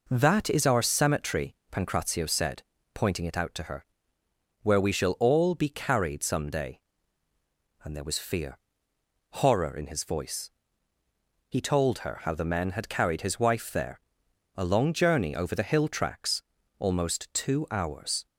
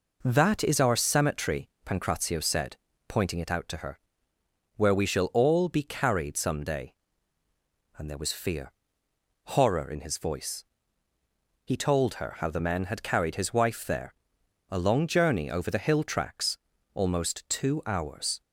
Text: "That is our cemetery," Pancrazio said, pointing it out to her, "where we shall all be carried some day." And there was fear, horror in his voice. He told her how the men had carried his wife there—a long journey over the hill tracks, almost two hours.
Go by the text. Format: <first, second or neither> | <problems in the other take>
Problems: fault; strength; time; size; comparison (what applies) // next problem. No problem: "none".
neither | none